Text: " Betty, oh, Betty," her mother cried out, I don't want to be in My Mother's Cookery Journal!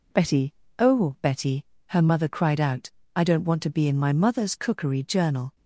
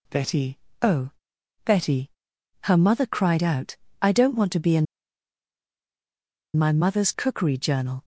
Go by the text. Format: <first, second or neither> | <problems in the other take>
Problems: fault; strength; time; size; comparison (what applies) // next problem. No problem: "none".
first | pauses between "in" and "My"; strong; at 4.8 s; 1.7 s long